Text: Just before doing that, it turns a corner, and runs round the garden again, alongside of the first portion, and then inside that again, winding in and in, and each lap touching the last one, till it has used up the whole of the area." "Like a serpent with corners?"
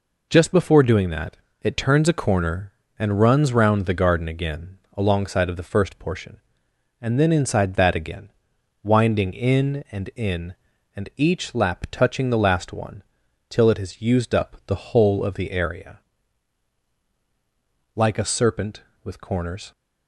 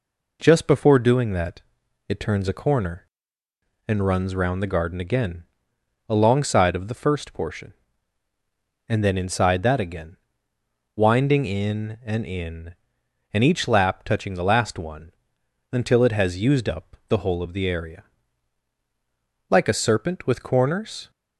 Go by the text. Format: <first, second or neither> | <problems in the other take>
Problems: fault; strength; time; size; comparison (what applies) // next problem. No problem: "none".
first | says "until" for "till"; at 15.7 s